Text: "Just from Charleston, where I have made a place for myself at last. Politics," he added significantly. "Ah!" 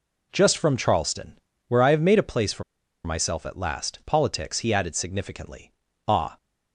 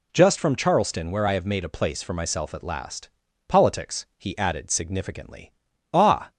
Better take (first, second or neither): second